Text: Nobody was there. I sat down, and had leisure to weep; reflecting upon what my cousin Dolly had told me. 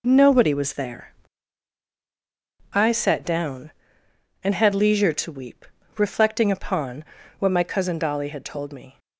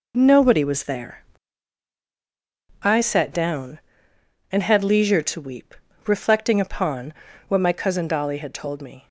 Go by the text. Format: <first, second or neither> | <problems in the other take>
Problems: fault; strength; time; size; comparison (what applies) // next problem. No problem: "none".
neither | pauses between "upon" and "what"; slight; the same in both